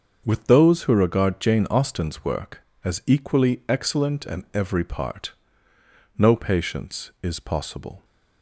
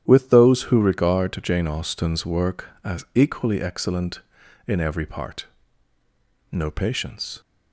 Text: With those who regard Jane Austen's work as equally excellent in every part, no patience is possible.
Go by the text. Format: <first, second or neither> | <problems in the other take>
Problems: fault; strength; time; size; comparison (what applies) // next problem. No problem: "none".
first | starts louder than the rest; strong; until 1.0 s; 10.5 dB; also in the first // stops before "is possible"; at 7.4 s